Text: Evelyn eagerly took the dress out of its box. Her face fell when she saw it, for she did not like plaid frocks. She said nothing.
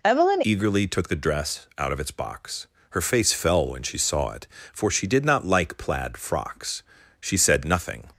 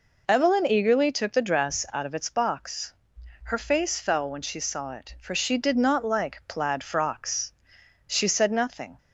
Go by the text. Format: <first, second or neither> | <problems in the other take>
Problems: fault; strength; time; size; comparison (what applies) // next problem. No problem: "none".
second | changes voice at "eagerly"; from 0.4 s on; 7.6 s long